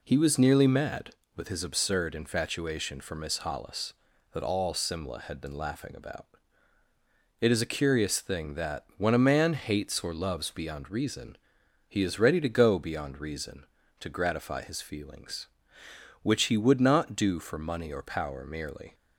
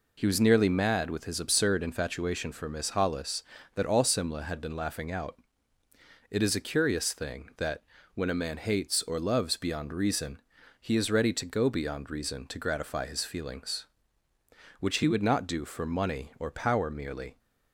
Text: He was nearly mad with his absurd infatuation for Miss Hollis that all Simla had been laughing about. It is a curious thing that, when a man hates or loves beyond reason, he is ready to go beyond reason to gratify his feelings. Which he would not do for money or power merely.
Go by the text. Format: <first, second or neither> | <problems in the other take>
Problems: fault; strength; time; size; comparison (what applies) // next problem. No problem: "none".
first | says "out" for "about"; at 5.1 s